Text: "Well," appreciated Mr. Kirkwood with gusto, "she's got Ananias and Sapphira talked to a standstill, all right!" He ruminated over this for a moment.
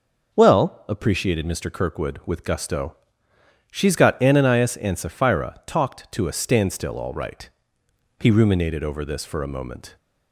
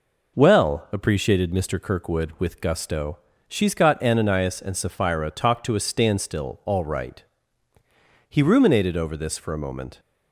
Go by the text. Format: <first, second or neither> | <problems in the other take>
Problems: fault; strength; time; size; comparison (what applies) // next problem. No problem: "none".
neither | none